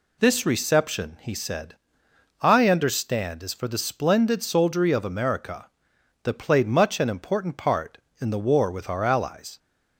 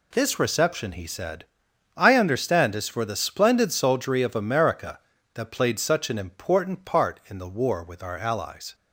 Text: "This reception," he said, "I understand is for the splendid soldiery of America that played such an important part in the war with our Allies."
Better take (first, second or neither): second